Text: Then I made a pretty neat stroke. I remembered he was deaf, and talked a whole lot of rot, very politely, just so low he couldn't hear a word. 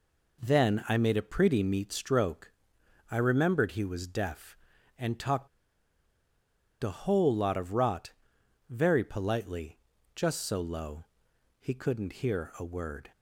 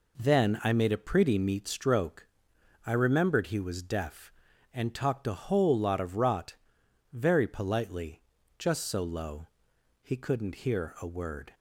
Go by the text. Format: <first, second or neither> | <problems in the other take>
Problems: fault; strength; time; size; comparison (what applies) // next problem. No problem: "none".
second | pauses between "talked" and "a"; strong; at 5.4 s; 1.3 s long // pauses between "low" and "he"; noticeable; at 11.0 s; 0.54 s long; noticeable in the second